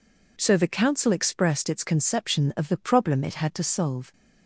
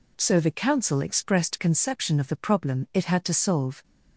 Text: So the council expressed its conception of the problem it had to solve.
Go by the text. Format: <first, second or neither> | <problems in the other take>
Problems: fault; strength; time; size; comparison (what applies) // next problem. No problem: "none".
first | skips "its"; at 1.5 s